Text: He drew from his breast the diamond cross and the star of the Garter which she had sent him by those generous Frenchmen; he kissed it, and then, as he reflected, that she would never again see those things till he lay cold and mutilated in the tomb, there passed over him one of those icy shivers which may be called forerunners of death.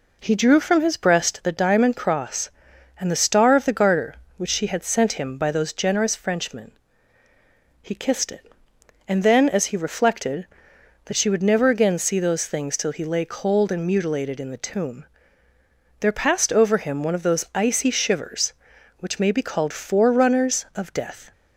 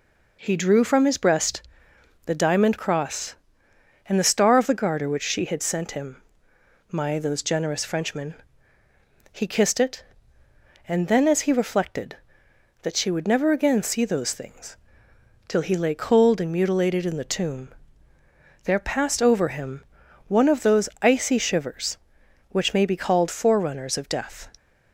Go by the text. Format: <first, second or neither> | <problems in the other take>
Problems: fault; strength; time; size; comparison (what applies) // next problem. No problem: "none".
first | pauses between "breast" and "the"; noticeable; at 1.6 s; 0.62 s long // says "my" for "by"; at 6.9 s // pauses between "things" and "till"; noticeable; at 14.7 s; 0.72 s long // pauses between "him" and "one"; at 19.8 s; 0.44 s long // pauses between "those" and "icy"; slight; at 20.8 s; 0.16 s long